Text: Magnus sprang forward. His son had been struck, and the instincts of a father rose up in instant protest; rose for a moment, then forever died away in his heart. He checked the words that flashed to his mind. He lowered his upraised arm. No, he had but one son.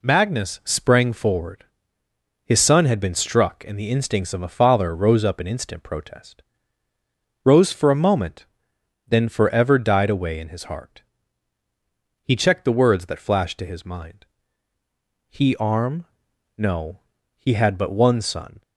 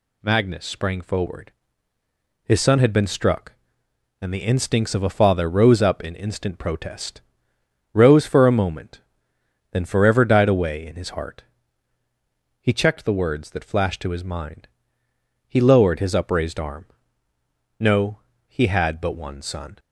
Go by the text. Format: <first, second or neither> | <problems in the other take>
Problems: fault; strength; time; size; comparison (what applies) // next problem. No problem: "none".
second | skips "lowered his upraised"; at 15.5 s